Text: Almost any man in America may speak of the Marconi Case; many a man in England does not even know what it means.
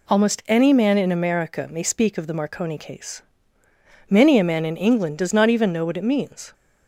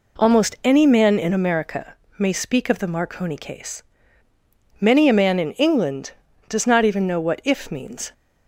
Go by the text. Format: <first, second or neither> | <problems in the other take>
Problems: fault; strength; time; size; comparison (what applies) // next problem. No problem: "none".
first | pauses between "America" and "may"; slight; at 1.9 s; 0.24 s long // says "if" for "it"; at 7.4 s